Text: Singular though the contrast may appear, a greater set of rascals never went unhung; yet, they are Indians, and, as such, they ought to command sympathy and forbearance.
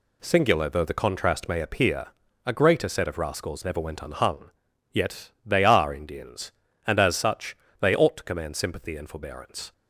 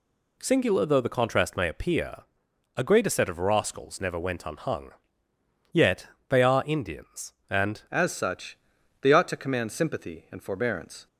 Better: first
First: none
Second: changes voice at "as"; from 7.9 s on; 3.1 s long

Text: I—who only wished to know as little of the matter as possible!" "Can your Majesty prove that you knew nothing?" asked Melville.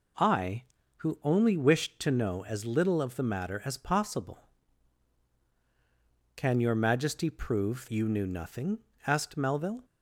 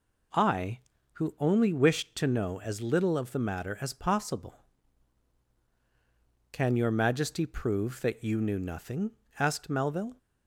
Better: second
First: skips "that"; at 7.8 s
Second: none

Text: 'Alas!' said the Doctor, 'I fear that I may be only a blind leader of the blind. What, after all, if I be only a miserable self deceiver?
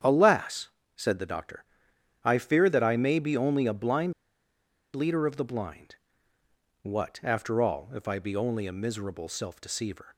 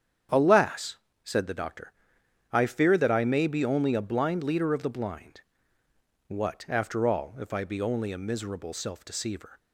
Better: second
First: starts louder than the rest; strong; until 1.3 s; 8.5 dB // pauses between "blind" and "leader"; noticeable; at 4.1 s; 0.83 s long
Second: starts louder than the rest; strong; until 1.6 s; 8.5 dB

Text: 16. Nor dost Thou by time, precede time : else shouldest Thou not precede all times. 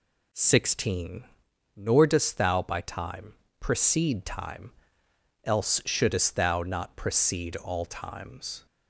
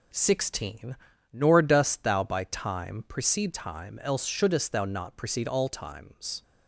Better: neither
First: none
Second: none

